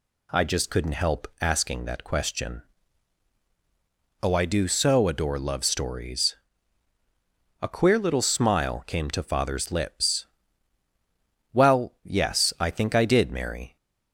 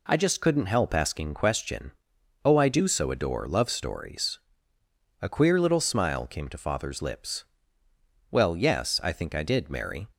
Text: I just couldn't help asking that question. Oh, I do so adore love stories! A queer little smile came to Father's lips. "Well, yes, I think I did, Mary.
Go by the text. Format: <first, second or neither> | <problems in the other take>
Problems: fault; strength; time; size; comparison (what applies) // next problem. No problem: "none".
first | skips "that"; at 1.3 s